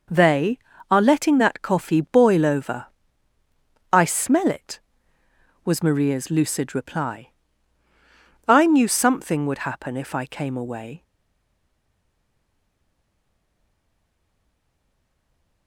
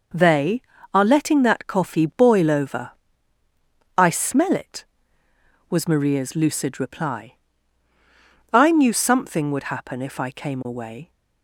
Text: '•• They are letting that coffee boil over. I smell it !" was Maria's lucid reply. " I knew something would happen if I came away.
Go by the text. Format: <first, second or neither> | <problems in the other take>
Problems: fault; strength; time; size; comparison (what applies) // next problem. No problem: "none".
second | stays silent after the last word; strong; from 11.0 s on; 4.6 s long